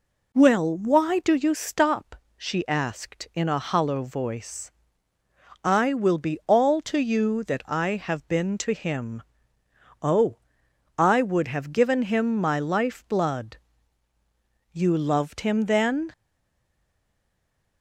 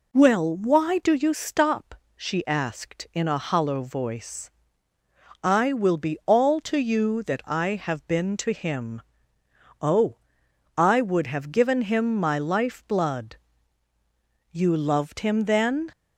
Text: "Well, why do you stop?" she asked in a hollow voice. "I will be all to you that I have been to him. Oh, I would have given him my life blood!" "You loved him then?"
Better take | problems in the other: second | stays silent after the last word; noticeable; from 16.1 s on; 1.7 s long

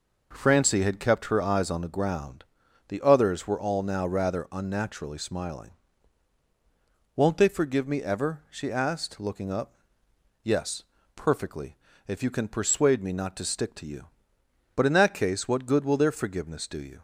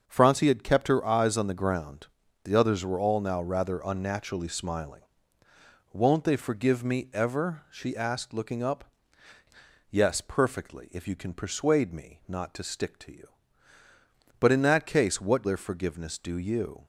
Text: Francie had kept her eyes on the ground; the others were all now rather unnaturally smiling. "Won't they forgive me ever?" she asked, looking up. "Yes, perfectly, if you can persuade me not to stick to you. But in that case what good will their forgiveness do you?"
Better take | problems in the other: first | starts louder than the rest; until 1.0 s; 6.5 dB // skips "good will"; at 15.4 s

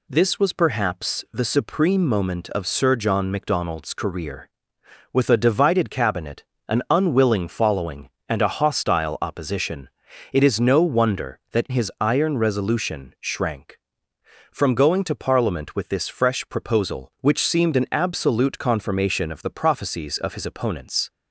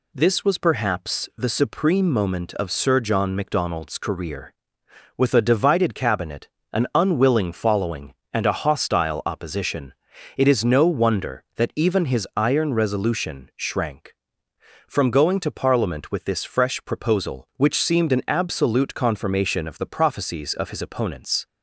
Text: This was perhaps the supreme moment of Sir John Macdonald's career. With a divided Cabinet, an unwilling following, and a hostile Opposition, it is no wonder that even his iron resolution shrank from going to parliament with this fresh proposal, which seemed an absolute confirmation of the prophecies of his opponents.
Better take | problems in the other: second | skips "even"; at 11.6 s

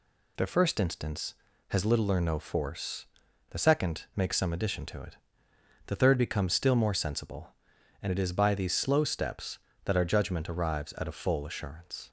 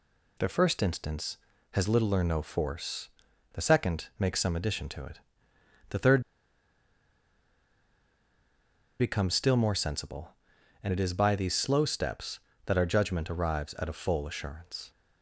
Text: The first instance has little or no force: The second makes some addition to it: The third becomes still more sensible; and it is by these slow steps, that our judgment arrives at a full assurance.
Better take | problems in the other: first | pauses between "third" and "becomes"; strong; at 6.2 s; 2.7 s long

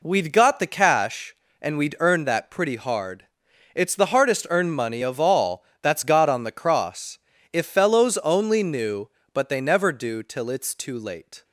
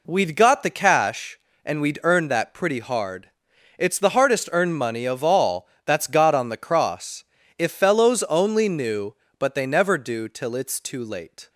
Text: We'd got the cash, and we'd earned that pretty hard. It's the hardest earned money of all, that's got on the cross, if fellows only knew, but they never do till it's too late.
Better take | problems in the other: neither | none

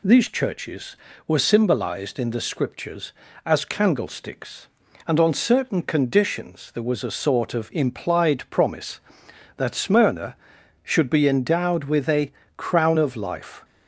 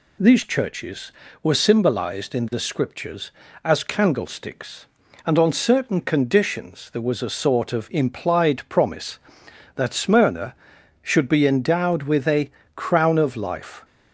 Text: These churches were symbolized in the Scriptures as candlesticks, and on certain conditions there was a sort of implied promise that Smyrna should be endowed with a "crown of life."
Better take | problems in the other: neither | pauses between "a" and "crown"; slight; the same in both

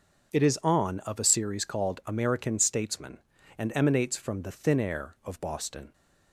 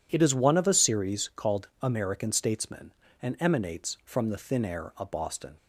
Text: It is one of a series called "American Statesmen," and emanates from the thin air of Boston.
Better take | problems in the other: second | starts louder than the rest; until 1.3 s; 6.5 dB // says "on" for "one"; at 0.6 s

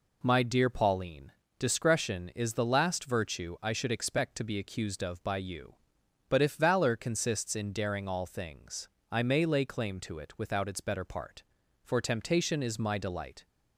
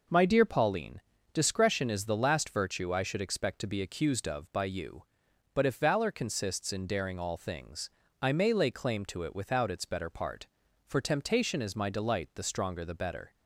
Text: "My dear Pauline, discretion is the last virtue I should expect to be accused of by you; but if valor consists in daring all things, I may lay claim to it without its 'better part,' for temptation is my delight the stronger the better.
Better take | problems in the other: second | stops before "the stronger the better"; at 13.4 s

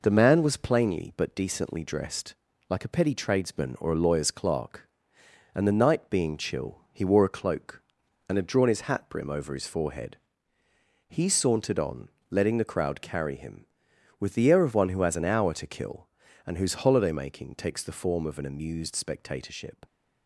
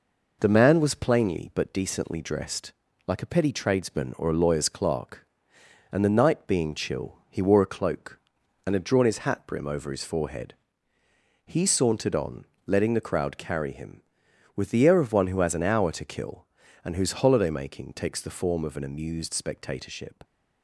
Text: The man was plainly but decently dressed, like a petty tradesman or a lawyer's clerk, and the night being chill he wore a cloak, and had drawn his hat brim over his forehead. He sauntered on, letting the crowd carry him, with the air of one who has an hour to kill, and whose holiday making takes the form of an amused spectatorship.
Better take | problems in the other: neither | none

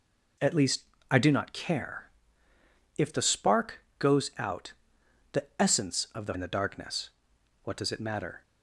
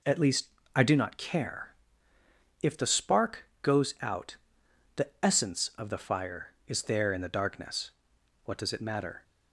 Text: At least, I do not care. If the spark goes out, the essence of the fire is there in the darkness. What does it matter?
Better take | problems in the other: second | skips "fire is there"; at 6.3 s

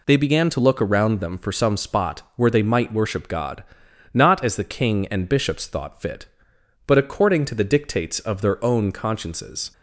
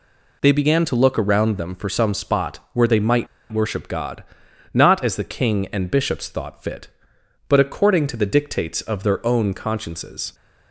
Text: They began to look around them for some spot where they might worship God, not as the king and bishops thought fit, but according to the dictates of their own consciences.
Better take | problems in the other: first | pauses between "might" and "worship"; slight; at 3.2 s; 0.25 s long

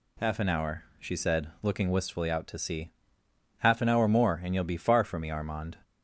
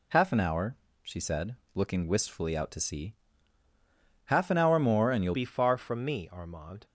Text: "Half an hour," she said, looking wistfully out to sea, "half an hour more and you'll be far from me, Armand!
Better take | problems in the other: first | changes voice at "be"; from 5.3 s on; 1.5 s long

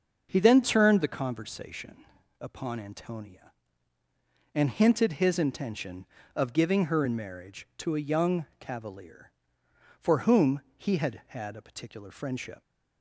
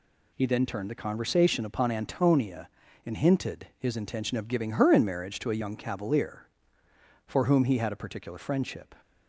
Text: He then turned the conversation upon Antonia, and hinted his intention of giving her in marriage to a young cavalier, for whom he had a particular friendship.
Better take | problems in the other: second | starts louder than the rest; until 1.3 s; 6 dB // pauses between "conversation" and "upon"; slight; at 2.0 s; 0.36 s long // pauses between "whom" and "he"; slight; at 10.6 s; 0.16 s long // says "had" twice; at 11.2 s

